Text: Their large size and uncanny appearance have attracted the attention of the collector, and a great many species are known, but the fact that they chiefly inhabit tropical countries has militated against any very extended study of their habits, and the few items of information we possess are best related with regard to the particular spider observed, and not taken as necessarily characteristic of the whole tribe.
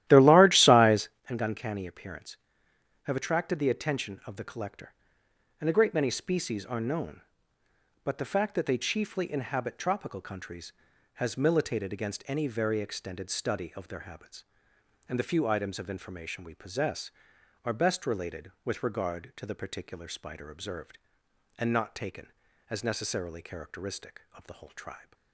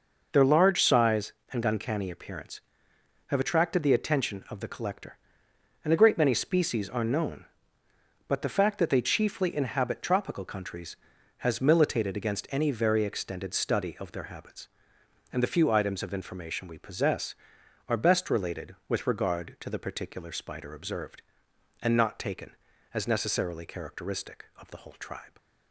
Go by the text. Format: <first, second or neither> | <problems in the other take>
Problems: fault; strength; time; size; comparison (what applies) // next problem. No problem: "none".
second | starts louder than the rest; strong; until 1.3 s; 14 dB